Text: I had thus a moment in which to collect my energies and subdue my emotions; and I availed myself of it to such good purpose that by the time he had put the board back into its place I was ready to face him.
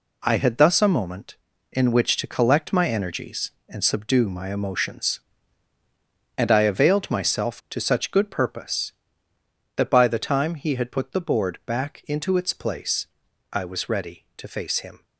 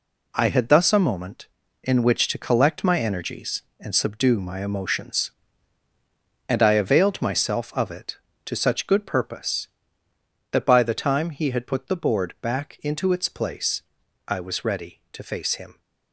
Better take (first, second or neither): second